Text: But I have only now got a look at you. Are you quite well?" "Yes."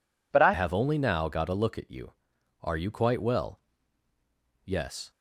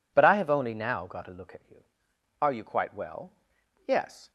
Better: second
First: changes voice at "have"; from 0.5 s on; 4.6 s long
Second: none

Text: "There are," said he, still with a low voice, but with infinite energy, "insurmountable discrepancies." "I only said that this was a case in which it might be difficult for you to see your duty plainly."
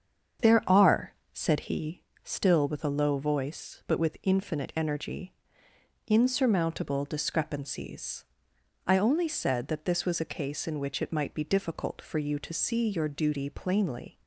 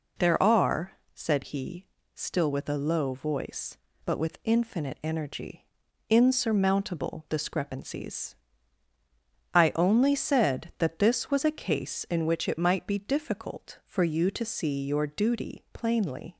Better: second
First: starts louder than the rest; strong; until 2.0 s; 7.5 dB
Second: none

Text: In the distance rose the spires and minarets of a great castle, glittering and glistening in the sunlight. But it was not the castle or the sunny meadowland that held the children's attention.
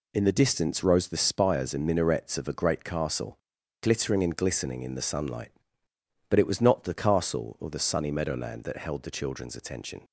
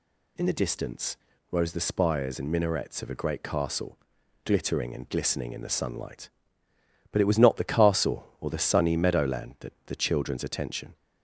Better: first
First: none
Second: pauses between "distance" and "rose"; slight; at 1.1 s; 0.34 s long // skips "held"; at 9.7 s

